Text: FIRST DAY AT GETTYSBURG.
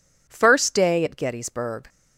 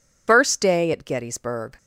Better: first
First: none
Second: loses the start of "FIRST"; at 0.2 s; 125 ms

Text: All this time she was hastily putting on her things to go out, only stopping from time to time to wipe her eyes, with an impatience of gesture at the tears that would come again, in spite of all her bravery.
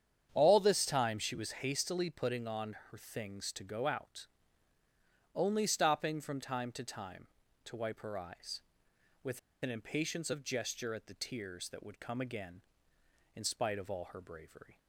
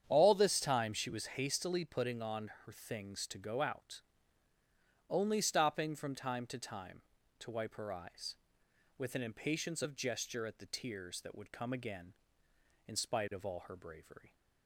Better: second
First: starts louder than the rest; strong; until 1.3 s; 8.5 dB // pauses between "on" and "her"; slight; at 2.7 s; 0.16 s long // pauses between "with" and "an"; slight; at 9.3 s; 0.24 s long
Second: starts louder than the rest; strong; until 1.1 s; 8.5 dB // pauses between "on" and "her"; slight; at 2.4 s; 0.16 s long

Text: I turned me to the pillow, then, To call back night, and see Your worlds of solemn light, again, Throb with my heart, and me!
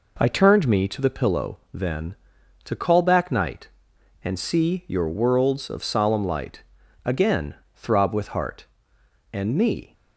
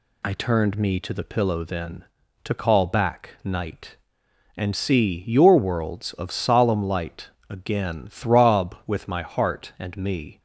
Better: second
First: skips "my"; at 8.2 s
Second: none

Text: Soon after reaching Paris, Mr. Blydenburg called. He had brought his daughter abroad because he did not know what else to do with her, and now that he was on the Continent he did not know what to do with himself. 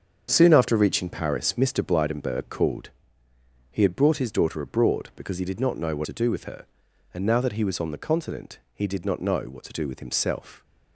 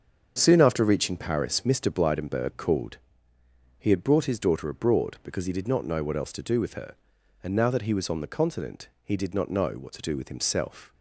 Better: second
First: starts louder than the rest; strong; until 1.3 s; 7 dB // skips "else"; at 6.0 s // pauses between "Continent" and "he"; slight; at 8.5 s; 0.16 s long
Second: starts louder than the rest; until 1.3 s; 7 dB // pauses between "Continent" and "he"; slight; at 8.8 s; 0.16 s long

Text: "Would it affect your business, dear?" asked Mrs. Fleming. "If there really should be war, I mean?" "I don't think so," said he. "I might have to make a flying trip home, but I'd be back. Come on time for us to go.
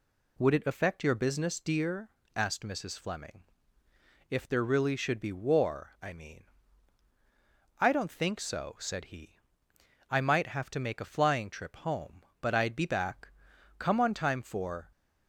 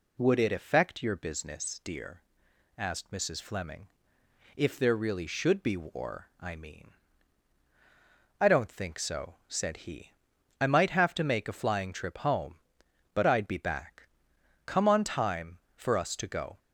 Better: second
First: stops before "us to go"; at 14.9 s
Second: none

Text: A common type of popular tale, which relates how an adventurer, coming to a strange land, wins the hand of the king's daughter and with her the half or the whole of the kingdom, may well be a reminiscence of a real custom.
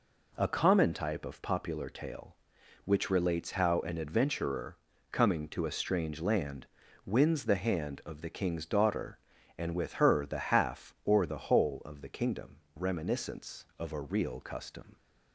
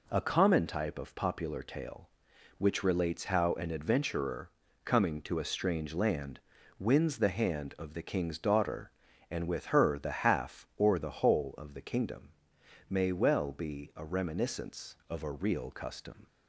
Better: second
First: skips "may well be a"; at 12.6 s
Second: none

